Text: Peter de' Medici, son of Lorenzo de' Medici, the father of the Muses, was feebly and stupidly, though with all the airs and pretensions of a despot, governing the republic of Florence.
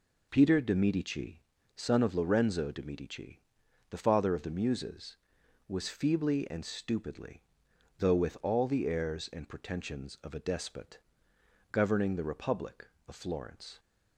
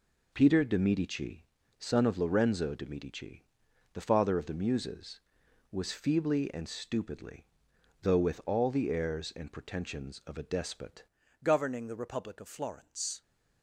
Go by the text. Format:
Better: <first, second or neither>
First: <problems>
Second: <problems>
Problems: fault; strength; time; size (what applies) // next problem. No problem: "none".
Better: first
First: none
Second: changes voice at "governing"; from 11.4 s on; 1.8 s long